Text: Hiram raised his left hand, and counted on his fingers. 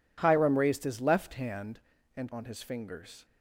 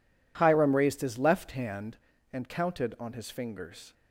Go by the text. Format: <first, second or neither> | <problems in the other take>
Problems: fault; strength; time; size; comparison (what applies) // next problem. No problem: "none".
second | skips "counted"; at 2.3 s